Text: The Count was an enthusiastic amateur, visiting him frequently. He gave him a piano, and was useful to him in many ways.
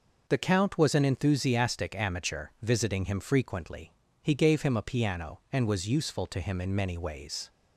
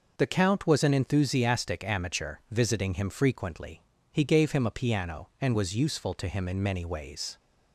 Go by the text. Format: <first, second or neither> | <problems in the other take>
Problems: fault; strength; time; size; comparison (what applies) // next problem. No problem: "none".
neither | none